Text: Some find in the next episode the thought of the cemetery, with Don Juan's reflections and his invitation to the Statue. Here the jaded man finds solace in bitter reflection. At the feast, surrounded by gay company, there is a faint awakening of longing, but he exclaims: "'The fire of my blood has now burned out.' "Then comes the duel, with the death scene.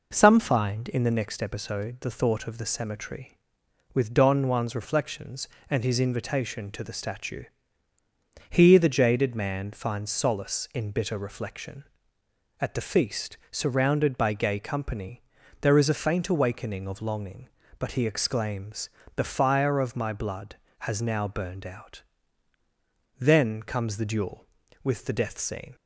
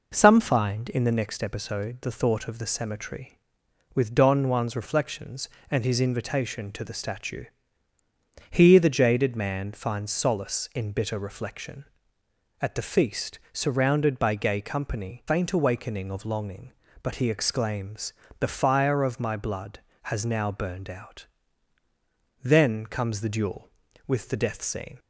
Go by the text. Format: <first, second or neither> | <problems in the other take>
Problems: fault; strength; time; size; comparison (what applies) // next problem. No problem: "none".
first | skips "there is a"; at 15.2 s